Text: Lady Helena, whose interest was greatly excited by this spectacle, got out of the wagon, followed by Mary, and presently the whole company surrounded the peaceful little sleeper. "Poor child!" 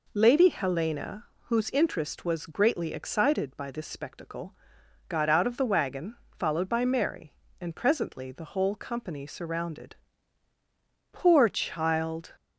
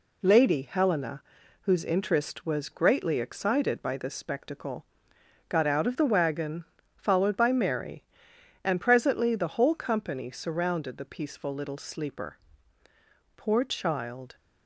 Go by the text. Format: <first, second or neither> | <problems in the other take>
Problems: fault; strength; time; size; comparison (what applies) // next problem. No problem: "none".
second | skips "the peaceful little sleeper"; at 10.5 s